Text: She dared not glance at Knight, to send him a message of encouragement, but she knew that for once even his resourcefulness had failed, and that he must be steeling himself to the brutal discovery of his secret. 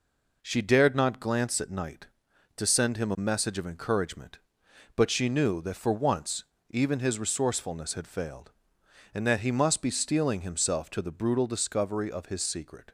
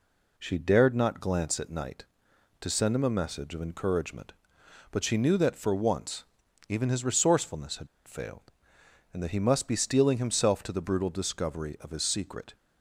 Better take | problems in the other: first | pauses between "once" and "even"; at 6.2 s; 0.44 s long; slight in the first // pauses between "had" and "failed"; slight; at 7.8 s; 0.19 s long

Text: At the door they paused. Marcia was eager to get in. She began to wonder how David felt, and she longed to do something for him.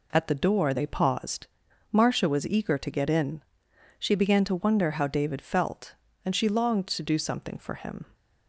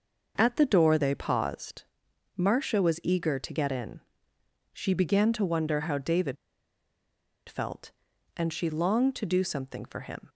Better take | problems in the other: first | pauses between "David" and "felt"; at 6.3 s; 1.1 s long

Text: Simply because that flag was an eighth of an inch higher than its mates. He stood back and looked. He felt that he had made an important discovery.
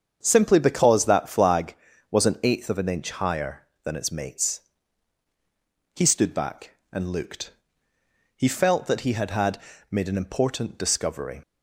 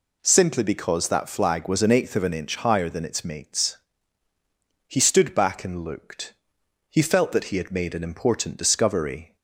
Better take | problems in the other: second | starts louder than the rest; strong; until 1.2 s; 7.5 dB // says "had" twice; at 9.3 s

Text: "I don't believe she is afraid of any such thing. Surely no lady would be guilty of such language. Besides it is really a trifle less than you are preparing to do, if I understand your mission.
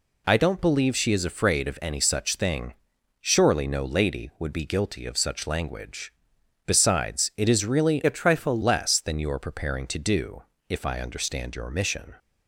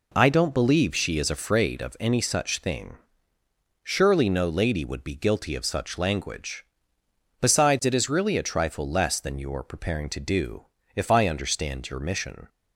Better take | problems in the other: second | changes voice from "a" to "trifle"; from 8.0 to 8.6 s; 0.6 s long

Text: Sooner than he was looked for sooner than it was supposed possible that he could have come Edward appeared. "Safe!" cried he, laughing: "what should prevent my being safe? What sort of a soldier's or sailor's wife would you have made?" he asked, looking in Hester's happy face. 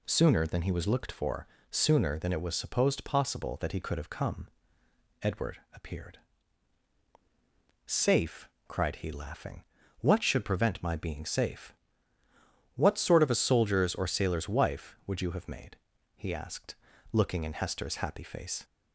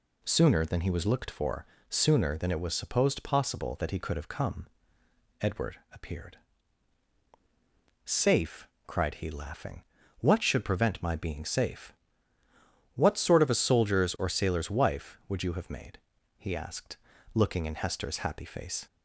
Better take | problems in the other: neither | pauses between "for" and "sooner"; slight; the same in both // pauses between "come" and "Edward"; noticeable; the same in both

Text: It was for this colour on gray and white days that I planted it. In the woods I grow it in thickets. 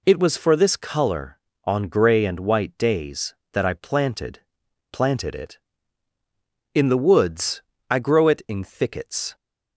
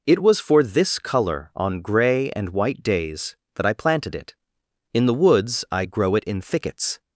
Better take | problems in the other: second | says "planted" twice; at 4.8 s // pauses between "woods" and "I"; slight; at 7.6 s; 0.26 s long

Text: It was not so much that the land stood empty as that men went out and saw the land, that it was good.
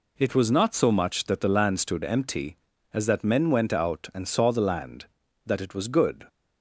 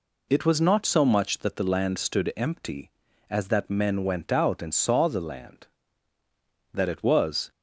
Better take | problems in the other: first | stops before "good"; at 7.5 s

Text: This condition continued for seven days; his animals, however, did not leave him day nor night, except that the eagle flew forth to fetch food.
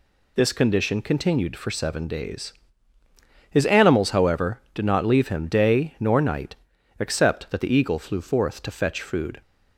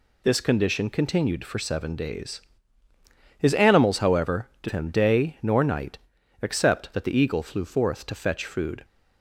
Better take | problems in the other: first | skips "not leave"; at 4.6 s

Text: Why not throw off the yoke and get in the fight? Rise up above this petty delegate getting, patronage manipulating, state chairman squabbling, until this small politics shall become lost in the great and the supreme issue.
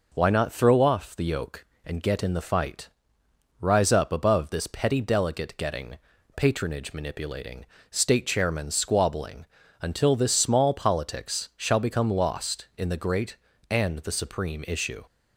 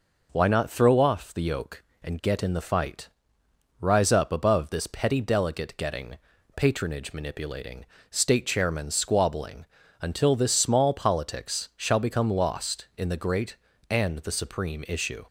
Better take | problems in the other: neither | none

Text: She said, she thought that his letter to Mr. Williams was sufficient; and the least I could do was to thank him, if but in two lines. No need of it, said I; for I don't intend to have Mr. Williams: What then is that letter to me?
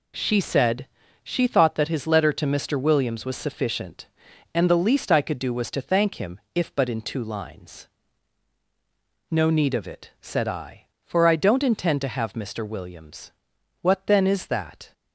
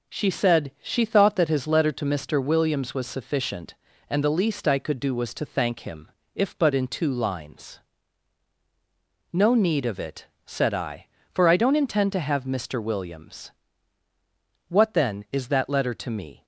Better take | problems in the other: second | stops before "letter to me"; at 14.9 s

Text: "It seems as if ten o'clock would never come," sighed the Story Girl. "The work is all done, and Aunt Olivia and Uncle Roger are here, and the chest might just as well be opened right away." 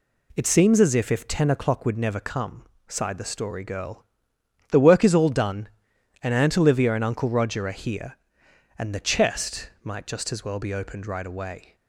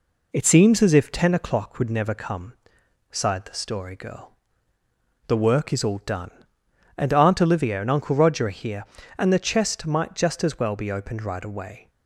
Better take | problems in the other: second | says "if" twice; at 1.1 s

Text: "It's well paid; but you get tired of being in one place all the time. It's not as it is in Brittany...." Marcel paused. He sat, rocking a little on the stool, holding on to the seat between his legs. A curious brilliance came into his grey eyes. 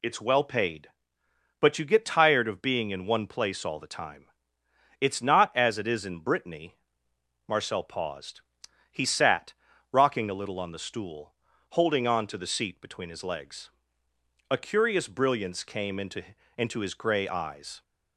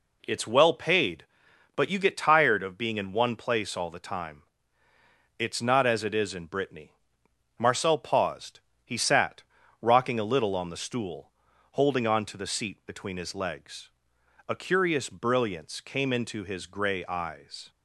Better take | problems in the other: second | says "into" twice; at 16.5 s

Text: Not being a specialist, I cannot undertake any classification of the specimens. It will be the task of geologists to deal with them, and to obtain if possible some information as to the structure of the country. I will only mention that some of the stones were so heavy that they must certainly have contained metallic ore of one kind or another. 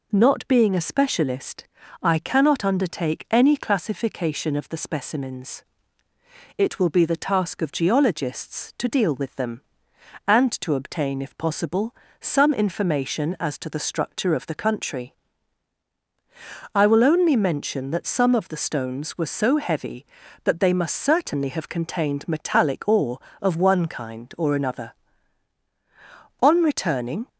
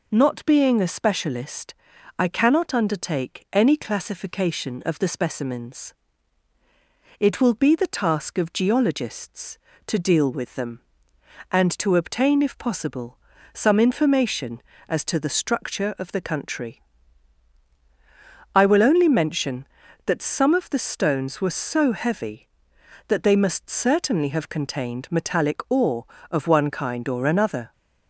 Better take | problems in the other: second | pauses between "possible" and "some"; slight; at 11.9 s; 0.26 s long; slight in the second // goes on to say "On returning"; noticeable; from 26.4 s on; 0.86 s long

